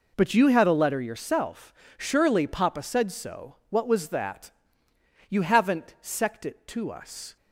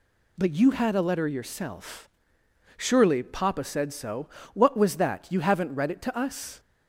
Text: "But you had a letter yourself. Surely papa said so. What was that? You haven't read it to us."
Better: second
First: says "sect" for "read"; at 6.0 s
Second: none

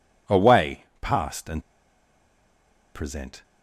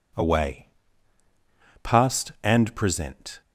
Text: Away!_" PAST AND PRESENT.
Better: second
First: pauses between "AND" and "PRESENT"; strong; at 1.6 s; 1.3 s long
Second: none

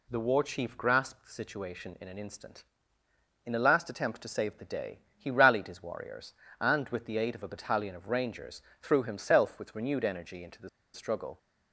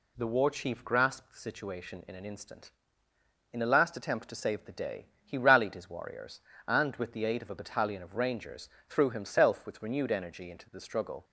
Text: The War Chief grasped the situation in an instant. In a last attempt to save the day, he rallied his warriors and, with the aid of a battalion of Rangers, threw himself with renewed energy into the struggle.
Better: second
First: pauses between "the" and "struggle"; slight; at 10.6 s; 0.24 s long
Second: none

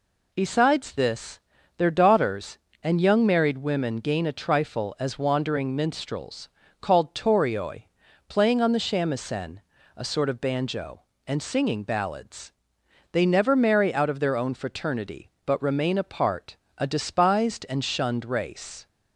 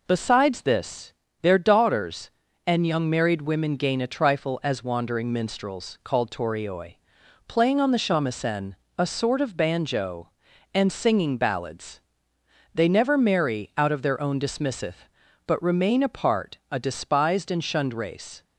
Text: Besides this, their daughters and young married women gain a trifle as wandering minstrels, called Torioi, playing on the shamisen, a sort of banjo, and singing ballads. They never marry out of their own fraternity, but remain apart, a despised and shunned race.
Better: first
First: none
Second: says "dismisseth" for "fraternity"; at 14.3 s

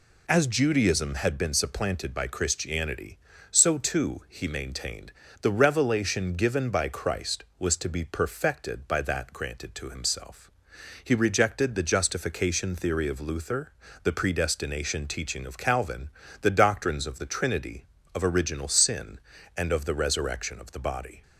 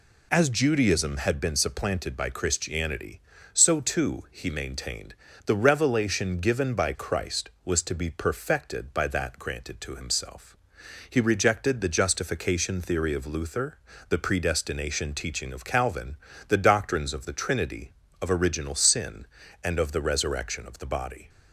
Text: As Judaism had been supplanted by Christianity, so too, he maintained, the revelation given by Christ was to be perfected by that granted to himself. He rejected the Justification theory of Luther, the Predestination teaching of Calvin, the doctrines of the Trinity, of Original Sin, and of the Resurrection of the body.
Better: neither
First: none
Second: none

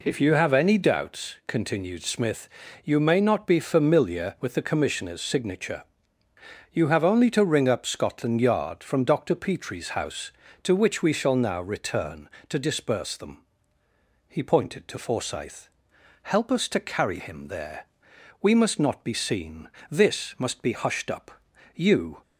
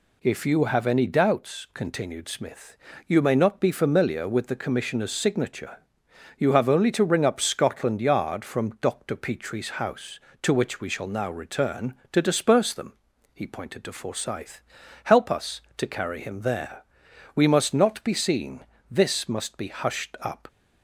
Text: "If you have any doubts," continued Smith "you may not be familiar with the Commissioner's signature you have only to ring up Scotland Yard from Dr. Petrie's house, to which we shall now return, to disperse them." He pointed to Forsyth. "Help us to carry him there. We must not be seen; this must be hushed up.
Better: second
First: pauses between "Smith" and "you"; slight; at 2.4 s; 0.34 s long // pauses between "signature" and "you"; noticeable; at 5.8 s; 0.88 s long // goes on to say "You"; slight; from 21.7 s on; 0.46 s long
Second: pauses between "Smith" and "you"; slight; at 2.7 s; 0.30 s long // pauses between "signature" and "you"; noticeable; at 5.7 s; 0.62 s long

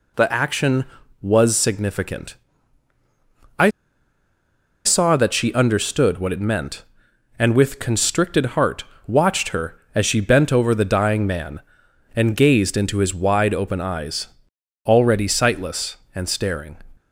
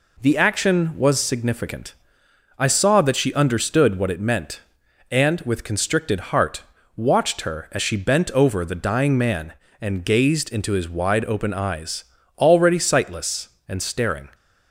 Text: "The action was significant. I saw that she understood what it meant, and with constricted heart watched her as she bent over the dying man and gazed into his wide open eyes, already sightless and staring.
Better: second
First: pauses between "I" and "saw"; at 3.6 s; 1.1 s long // pauses between "heart" and "watched"; slight; at 8.8 s; 0.22 s long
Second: pauses between "heart" and "watched"; slight; at 6.6 s; 0.32 s long

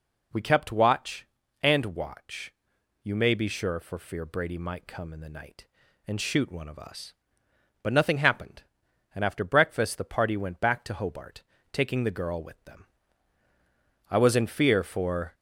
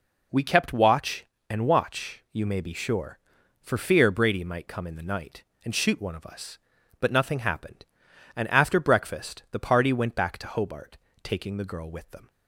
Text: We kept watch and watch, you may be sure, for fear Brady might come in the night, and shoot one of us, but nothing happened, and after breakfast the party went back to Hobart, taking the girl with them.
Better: second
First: goes on to say "I was in fear for"; noticeable; from 14.1 s on; 1.2 s long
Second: none

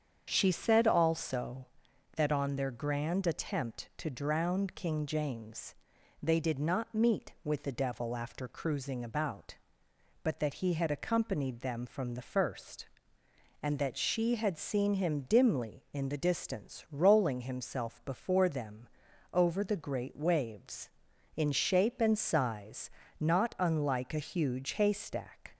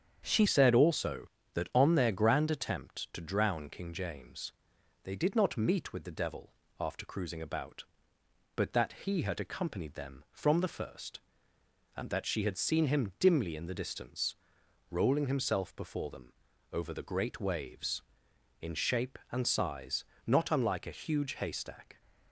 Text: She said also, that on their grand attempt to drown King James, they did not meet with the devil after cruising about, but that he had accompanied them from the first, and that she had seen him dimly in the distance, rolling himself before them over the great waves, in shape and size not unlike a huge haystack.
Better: first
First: starts louder than the rest; strong; until 1.3 s; 7.5 dB // pauses between "them" and "over"; at 18.8 s; 0.44 s long // pauses between "size" and "not"; slight; at 22.8 s; 0.32 s long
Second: starts louder than the rest; strong; until 1.2 s; 8 dB // changes voice at "said"; from 0.4 s on; 21.6 s long // pauses between "devil" and "after"; slight; at 6.5 s; 0.28 s long // pauses between "them" and "over"; at 16.3 s; 0.40 s long // pauses between "size" and "not"; slight; at 20.0 s; 0.22 s long

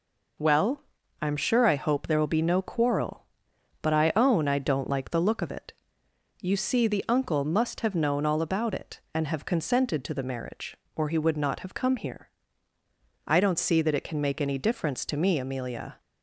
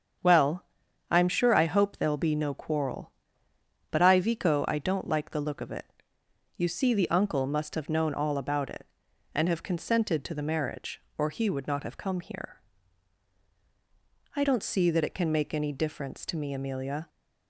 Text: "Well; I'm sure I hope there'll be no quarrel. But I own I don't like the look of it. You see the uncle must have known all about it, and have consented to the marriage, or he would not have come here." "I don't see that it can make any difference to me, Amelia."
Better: first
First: none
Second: starts louder than the rest; strong; until 1.6 s; 7.5 dB // says "vico" for "own"; at 4.1 s

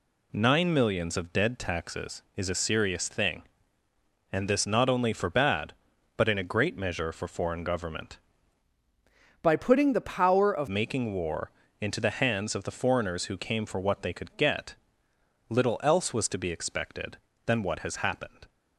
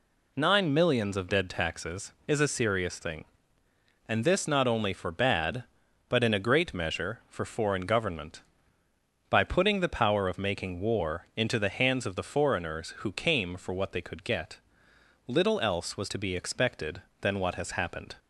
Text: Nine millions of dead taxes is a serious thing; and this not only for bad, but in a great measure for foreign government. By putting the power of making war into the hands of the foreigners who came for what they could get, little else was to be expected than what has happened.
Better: second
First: changes voice from "By" to "of"; from 9.4 to 10.6 s; 1.2 s long // pauses between "war" and "into"; slight; at 11.5 s; 0.30 s long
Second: none

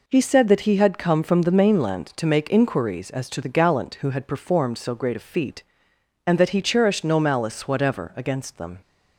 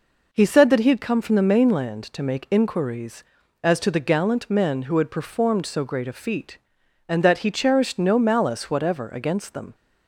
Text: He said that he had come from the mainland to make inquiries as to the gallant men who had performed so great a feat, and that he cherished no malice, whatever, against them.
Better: second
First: skips "men"; at 3.9 s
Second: none

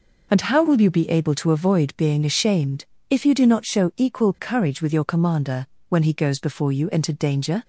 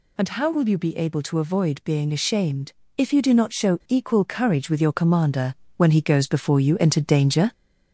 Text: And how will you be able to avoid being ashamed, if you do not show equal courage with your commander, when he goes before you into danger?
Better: first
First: none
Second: gets louder; slight; throughout; 2.5 dB

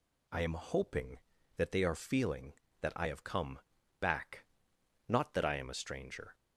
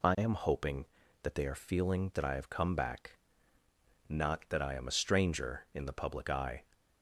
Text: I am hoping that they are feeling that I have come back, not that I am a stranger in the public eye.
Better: second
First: pauses between "come" and "back"; at 3.5 s; 0.40 s long // stops before "in the public eye"; at 6.3 s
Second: none

